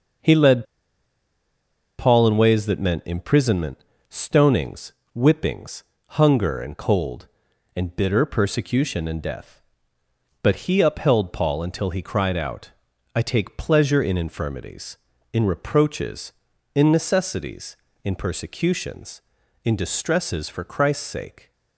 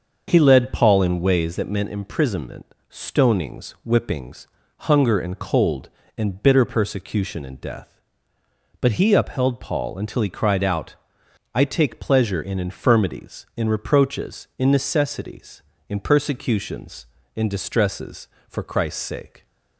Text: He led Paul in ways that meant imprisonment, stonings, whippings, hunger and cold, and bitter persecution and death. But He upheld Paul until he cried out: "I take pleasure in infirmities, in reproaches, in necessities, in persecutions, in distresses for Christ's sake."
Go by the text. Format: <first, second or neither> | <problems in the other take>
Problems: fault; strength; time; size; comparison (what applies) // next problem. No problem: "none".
second | starts louder than the rest; until 2.5 s; 6.5 dB; also in the second // pauses between "led" and "Paul"; strong; at 0.6 s; 1.3 s long